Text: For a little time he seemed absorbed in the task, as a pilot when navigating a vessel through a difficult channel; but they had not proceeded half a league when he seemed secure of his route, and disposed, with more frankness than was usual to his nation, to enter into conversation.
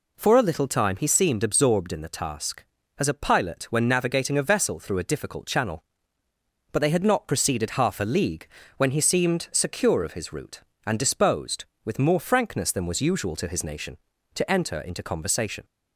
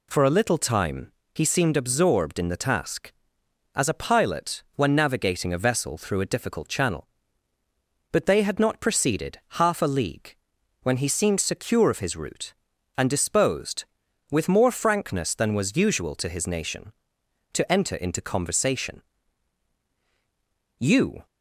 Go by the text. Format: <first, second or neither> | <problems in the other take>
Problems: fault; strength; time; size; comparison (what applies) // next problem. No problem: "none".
first | pauses between "time" and "he"; slight; at 1.1 s; 0.24 s long // pauses between "proceeded" and "half"; slight; at 9.3 s; 0.22 s long // pauses between "league" and "when"; noticeable; at 10.3 s; 0.46 s long; slight in the first // goes on to say "You"; slight; from 20.7 s on; 0.46 s long